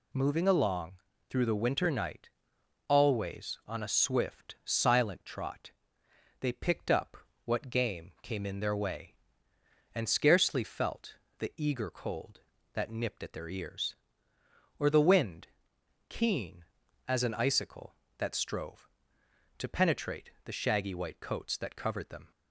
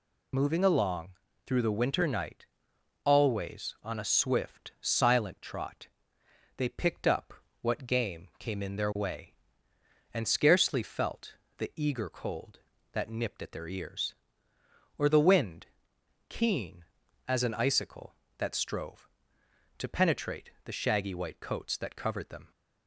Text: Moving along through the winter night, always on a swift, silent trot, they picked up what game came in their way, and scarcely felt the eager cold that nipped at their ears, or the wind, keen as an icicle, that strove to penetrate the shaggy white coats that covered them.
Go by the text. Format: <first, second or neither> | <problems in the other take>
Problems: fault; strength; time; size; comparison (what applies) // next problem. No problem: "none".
first | loses the start of "Moving"; at 0.3 s; 35 ms // pauses between "along" and "through"; slight; at 1.0 s; 0.36 s long; slight in the first // pauses between "up" and "what"; slight; at 7.3 s; 0.30 s long; slight in the first // pauses between "felt" and "the"; slight; at 11.3 s; 0.26 s long; slight in the first